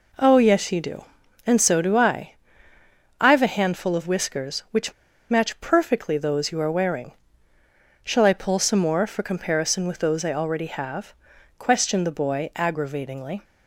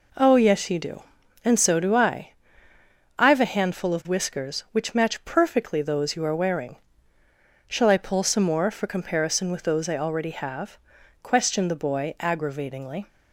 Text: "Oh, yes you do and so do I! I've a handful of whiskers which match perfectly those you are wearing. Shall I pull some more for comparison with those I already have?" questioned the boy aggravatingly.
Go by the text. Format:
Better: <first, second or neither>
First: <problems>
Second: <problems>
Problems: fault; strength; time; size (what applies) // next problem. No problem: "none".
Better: second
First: pauses between "which" and "match"; at 4.9 s; 0.36 s long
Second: none